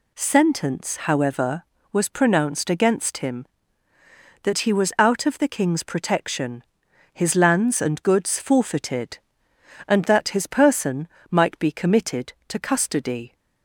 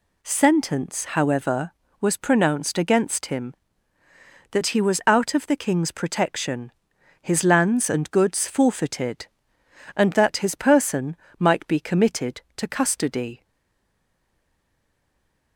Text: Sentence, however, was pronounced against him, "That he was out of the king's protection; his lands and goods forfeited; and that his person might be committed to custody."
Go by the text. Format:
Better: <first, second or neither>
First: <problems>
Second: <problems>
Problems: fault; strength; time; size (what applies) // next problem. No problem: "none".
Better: first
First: pauses between "person" and "might"; slight; at 11.0 s; 0.24 s long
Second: pauses between "person" and "might"; slight; at 11.1 s; 0.24 s long // stays silent after the last word; from 13.4 s on; 2.1 s long